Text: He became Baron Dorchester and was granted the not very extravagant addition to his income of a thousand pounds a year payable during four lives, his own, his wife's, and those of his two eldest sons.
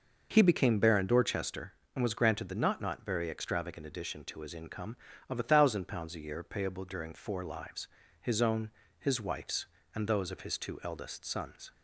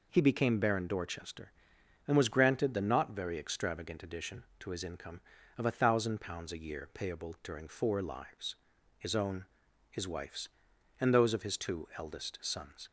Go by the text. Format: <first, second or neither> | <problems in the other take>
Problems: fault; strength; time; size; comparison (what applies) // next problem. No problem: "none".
second | says "not" twice; at 2.7 s